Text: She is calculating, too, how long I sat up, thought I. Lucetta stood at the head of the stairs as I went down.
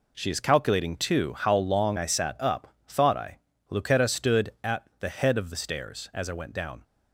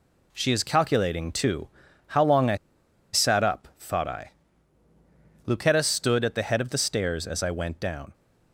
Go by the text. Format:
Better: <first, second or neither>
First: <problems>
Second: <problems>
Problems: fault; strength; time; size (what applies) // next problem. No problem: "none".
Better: first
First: none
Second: pauses between "I" and "sat"; noticeable; at 2.5 s; 0.57 s long